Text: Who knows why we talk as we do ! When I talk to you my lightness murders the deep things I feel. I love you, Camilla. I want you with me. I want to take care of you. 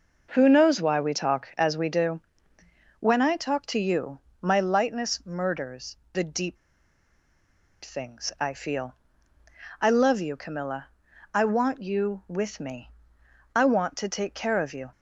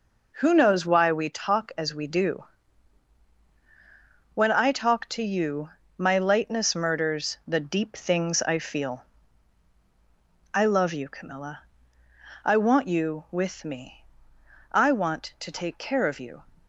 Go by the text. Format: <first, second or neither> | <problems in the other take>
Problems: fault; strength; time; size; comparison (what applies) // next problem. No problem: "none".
second | pauses between "you" and "my"; slight; at 4.1 s; 0.22 s long; slight in the second // pauses between "murders" and "the"; slight; at 5.9 s; 0.18 s long // pauses between "deep" and "things"; strong; at 6.5 s; 1.2 s long